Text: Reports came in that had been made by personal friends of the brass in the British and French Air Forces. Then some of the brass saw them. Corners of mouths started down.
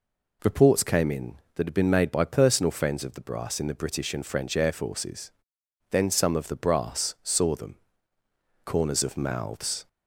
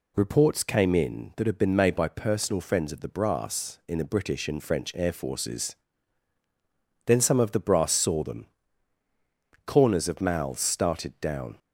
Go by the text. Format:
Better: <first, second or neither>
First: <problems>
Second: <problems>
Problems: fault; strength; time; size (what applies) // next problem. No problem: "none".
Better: second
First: stops before "started down"; at 9.8 s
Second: none